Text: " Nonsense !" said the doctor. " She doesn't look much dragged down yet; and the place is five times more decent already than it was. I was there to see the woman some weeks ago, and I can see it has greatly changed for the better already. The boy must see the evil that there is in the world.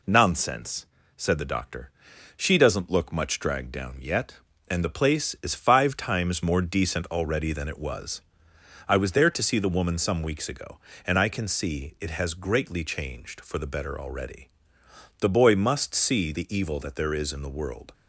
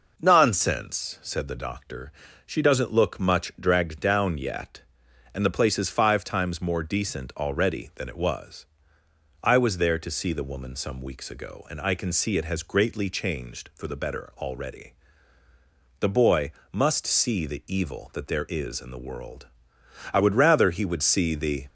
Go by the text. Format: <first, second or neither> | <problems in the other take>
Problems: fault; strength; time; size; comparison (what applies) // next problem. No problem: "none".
first | pauses between "boy" and "must"; slight; at 16.5 s; 0.22 s long // goes on to say "I would rather he would see the"; from 20.1 s on; 1.5 s long